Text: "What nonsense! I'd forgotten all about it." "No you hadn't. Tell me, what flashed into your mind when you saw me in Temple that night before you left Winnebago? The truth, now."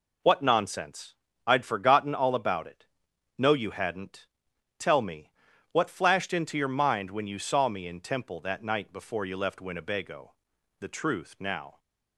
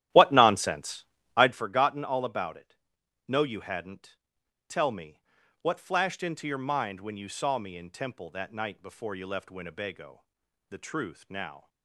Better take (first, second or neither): first